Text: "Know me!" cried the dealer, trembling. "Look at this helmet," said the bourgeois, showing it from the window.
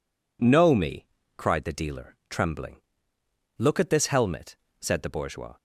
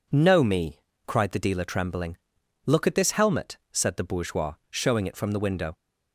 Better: second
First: stops before "showing it from the window"; at 5.5 s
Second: none

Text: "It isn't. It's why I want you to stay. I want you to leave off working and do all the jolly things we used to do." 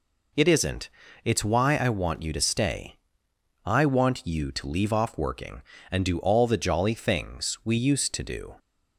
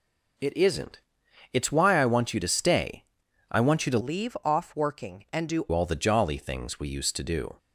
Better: first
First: none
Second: changes voice from "leave" to "do"; from 4.0 to 5.6 s; 1.6 s long

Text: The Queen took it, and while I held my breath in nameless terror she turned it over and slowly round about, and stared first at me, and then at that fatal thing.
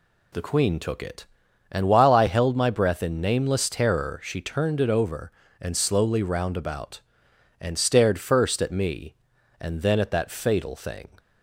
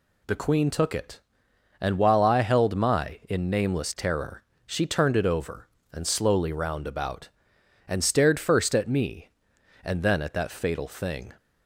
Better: first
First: none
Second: skips "breath"; at 3.2 s // pauses between "terror" and "she"; slight; at 4.4 s; 0.24 s long

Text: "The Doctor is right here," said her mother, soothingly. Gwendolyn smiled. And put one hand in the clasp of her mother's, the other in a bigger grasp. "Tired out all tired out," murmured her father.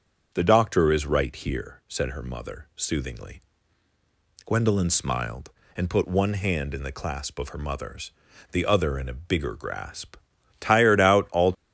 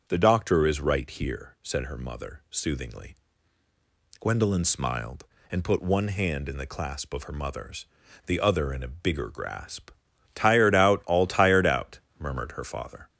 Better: second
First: starts louder than the rest; strong; until 1.3 s; 7.5 dB // stops before "tired out murmured her father"; at 11.5 s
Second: starts louder than the rest; strong; until 1.1 s; 7.5 dB

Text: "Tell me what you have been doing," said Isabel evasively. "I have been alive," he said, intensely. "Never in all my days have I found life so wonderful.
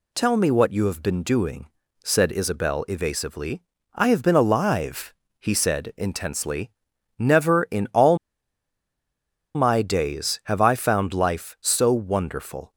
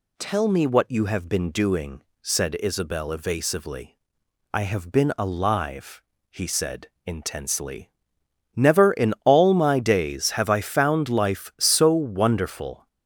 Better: second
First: pauses between "all" and "my"; strong; at 8.1 s; 1.3 s long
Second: none

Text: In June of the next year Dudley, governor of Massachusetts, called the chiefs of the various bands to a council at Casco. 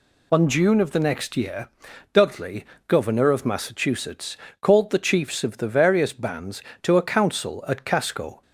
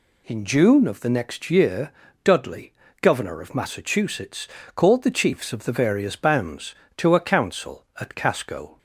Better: second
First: says "On" for "In"; at 0.3 s // pauses between "year" and "Dudley"; at 1.6 s; 0.44 s long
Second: pauses between "year" and "Dudley"; slight; at 1.9 s; 0.32 s long

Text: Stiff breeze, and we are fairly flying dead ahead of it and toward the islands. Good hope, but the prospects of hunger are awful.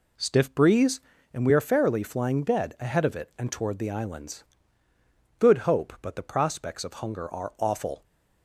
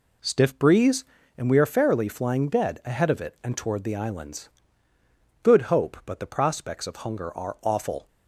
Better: neither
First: none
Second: none

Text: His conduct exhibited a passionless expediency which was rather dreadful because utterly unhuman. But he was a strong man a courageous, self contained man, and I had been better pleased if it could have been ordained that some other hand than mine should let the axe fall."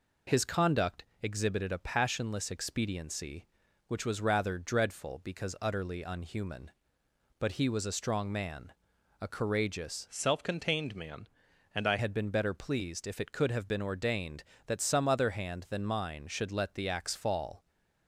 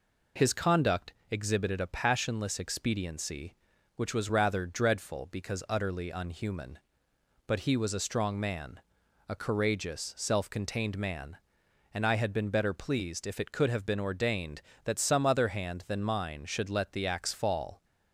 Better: second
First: pauses between "conduct" and "exhibited"; slight; at 1.0 s; 0.18 s long // pauses between "man" and "a"; noticeable; at 8.7 s; 0.48 s long // changes voice from "self" to "I"; from 10.0 to 11.9 s; 1.9 s long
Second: pauses between "conduct" and "exhibited"; slight; at 1.1 s; 0.18 s long // pauses between "man" and "a"; noticeable; at 8.8 s; 0.48 s long

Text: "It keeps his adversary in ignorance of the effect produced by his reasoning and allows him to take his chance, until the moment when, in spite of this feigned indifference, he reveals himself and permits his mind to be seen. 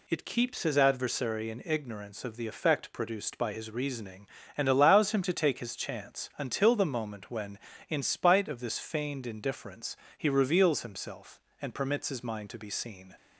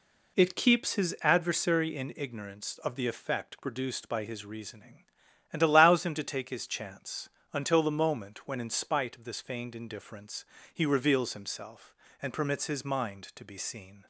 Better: neither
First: none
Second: none

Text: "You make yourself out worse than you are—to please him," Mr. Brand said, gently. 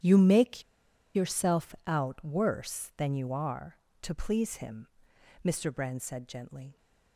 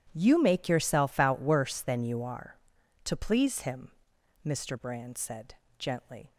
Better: second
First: starts louder than the rest; strong; until 1.5 s; 10.5 dB // pauses between "make" and "yourself"; noticeable; at 0.6 s; 0.52 s long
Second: none

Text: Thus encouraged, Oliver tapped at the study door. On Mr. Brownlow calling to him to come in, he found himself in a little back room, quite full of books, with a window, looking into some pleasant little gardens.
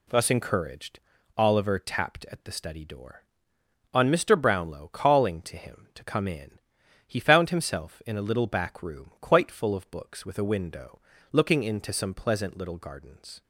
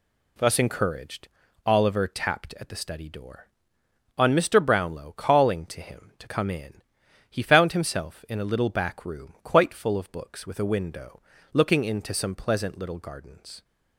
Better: neither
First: none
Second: none

